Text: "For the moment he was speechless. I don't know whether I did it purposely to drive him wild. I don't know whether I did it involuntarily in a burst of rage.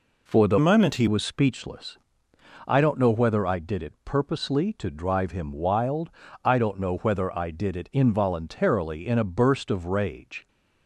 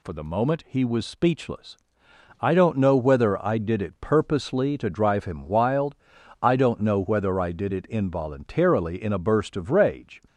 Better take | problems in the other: second | changes voice from "moment" to "he"; from 0.5 to 1.0 s; 0.5 s long

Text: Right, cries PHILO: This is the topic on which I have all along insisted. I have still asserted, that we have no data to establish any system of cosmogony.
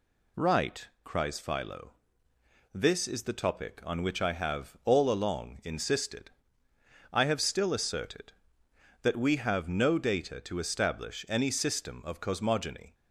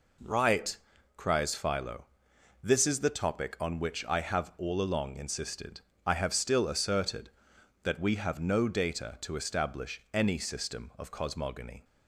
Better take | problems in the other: neither | none

